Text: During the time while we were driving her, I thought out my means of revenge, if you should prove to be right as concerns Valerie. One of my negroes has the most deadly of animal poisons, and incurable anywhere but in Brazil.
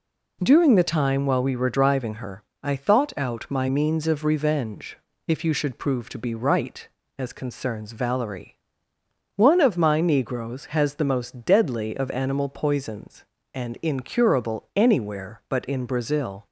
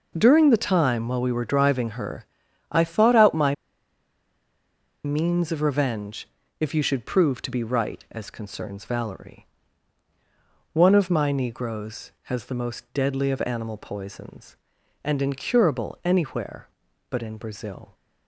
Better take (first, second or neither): first